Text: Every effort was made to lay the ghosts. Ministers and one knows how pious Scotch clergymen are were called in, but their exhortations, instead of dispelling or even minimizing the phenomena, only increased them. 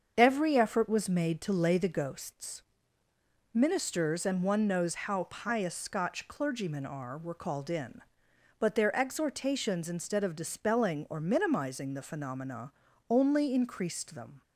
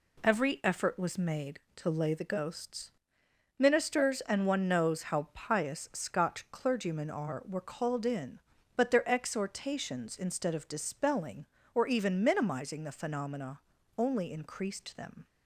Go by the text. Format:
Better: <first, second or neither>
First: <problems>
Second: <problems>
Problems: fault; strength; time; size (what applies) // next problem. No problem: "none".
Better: second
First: starts louder than the rest; until 1.1 s; 7 dB // skips "even"; at 11.2 s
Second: none